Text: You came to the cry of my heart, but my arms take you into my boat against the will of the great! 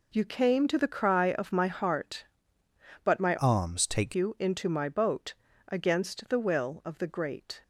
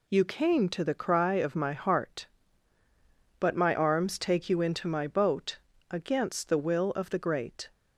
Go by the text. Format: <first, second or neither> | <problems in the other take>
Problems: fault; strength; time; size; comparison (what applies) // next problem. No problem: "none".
second | changes voice from "arms" to "take"; from 3.3 to 4.1 s; 0.8 s long // pauses between "boat" and "against"; slight; at 5.3 s; 0.34 s long; slight in the second